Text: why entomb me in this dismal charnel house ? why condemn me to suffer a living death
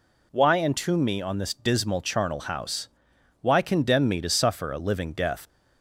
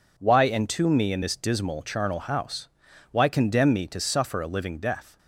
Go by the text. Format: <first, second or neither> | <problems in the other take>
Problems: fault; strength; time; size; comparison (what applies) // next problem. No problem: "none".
second | says "on" for "in"; at 1.2 s